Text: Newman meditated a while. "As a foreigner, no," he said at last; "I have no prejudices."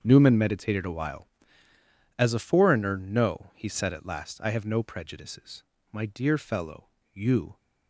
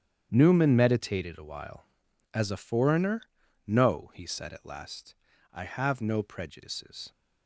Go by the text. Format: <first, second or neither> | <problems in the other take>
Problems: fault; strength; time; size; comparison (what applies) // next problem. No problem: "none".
second | starts louder than the rest; strong; until 1.0 s; 7.5 dB; strong in the second // goes on to say "My dear fellow you"; from 5.9 s on; 1.6 s long